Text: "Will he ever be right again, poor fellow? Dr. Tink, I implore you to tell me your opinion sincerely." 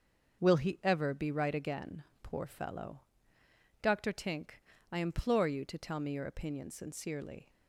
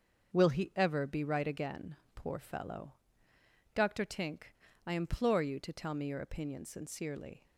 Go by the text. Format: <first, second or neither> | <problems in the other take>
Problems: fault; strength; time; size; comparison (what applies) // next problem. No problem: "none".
neither | starts louder than the rest; the same in both